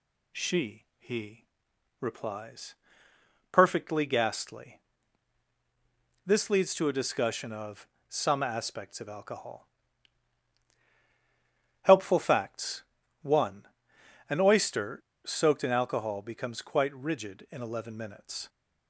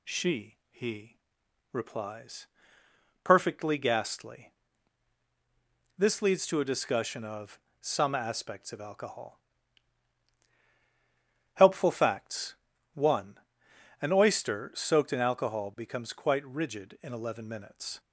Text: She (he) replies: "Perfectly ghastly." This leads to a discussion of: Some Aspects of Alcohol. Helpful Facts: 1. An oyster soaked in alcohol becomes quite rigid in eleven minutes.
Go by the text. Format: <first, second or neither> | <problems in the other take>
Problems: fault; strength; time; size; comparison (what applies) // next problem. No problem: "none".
second | pauses between "oyster" and "soaked"; slight; at 14.9 s; 0.29 s long